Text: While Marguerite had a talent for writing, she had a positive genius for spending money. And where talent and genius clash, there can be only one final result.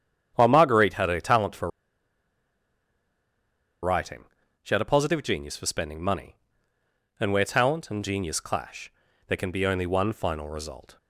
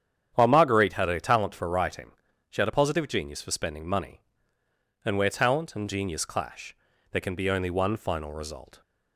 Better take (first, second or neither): second